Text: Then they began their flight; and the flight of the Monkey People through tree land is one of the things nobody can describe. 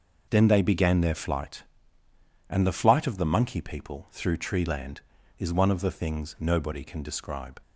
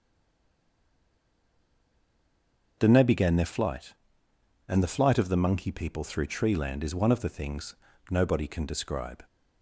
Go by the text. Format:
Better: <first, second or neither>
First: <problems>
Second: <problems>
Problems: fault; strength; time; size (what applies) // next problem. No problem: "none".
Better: first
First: none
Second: stays silent before the first word; strong; until 2.7 s; 2.7 s long // starts louder than the rest; until 3.7 s; 6.5 dB // pauses between "things" and "nobody"; slight; at 7.7 s; 0.34 s long